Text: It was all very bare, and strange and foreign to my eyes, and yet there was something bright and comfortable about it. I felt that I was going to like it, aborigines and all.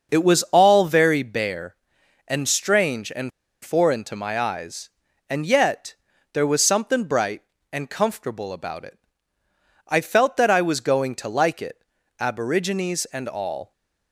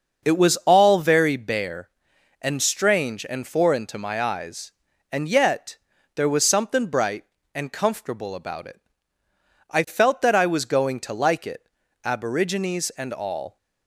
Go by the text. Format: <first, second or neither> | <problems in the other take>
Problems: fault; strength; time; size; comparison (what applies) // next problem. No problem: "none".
second | starts louder than the rest; noticeable; until 1.1 s; 6 dB; noticeable in the second // pauses between "and" and "foreign"; slight; at 3.3 s; 0.33 s long // pauses between "yet" and "there"; at 5.9 s; 0.40 s long; also in the second